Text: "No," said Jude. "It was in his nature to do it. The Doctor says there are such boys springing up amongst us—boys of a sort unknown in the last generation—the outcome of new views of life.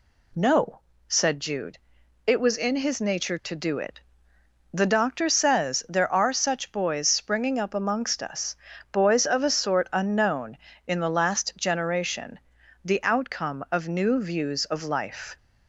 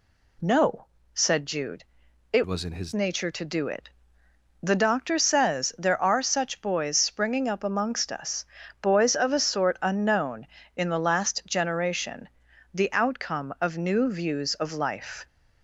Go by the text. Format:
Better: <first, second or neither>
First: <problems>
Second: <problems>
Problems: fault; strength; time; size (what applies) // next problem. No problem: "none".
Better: first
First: none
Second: changes voice from "was" to "his"; from 2.4 to 2.9 s; 0.5 s long